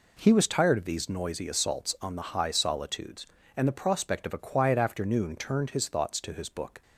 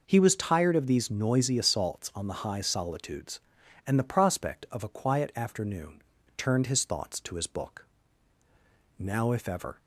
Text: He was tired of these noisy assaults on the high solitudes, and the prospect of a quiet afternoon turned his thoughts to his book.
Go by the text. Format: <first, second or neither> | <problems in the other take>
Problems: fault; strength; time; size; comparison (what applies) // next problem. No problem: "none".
first | pauses between "afternoon" and "turned"; slight; at 6.0 s; 0.34 s long // goes on to say "Now if ever"; noticeable; from 8.9 s on; 0.80 s long